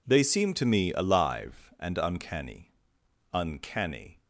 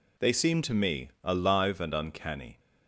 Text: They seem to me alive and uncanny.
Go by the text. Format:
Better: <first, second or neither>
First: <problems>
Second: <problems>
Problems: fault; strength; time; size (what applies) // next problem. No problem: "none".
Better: second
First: says "uncanny" twice; at 3.3 s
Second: none